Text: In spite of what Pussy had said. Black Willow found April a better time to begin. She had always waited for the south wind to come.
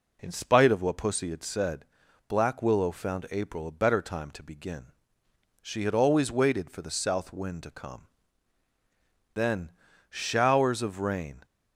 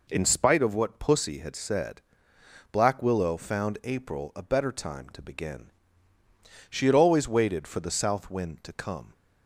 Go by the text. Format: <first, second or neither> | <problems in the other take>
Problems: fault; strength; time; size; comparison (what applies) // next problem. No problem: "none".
second | goes on to say "Then Showers of rain"; strong; from 9.3 s on; 2.1 s long